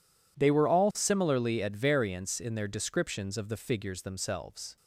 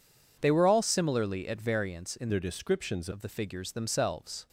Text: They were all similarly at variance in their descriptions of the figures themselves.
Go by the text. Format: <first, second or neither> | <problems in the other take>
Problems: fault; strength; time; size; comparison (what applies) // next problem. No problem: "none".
first | changes voice from "their" to "descriptions"; from 2.2 to 3.0 s; 0.8 s long